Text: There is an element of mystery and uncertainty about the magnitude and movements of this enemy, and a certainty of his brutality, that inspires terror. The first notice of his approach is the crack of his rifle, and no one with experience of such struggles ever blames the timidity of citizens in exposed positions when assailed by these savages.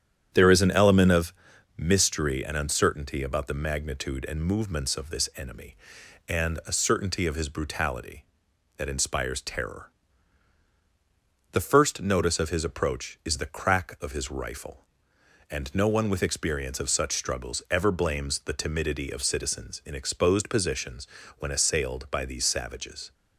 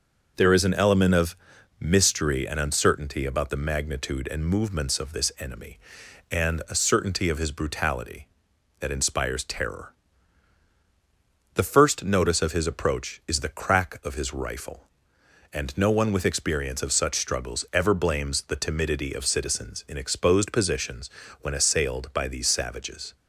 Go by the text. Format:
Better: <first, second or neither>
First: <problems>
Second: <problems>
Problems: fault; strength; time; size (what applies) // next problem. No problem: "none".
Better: second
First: starts louder than the rest; strong; until 1.2 s; 9.5 dB // pauses between "of" and "mystery"; at 1.3 s; 0.44 s long // pauses between "positions" and "when"; slight; at 21.0 s; 0.32 s long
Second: pauses between "of" and "mystery"; at 1.3 s; 0.44 s long // pauses between "positions" and "when"; slight; at 21.0 s; 0.32 s long